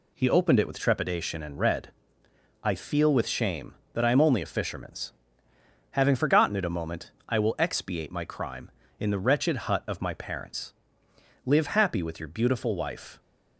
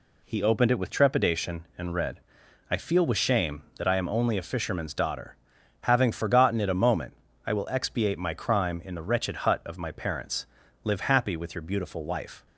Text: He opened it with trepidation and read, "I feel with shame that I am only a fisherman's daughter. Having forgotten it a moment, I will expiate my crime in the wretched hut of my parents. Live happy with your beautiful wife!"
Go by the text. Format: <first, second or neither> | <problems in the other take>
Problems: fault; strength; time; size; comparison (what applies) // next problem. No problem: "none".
second | skips "daughter"; at 5.5 s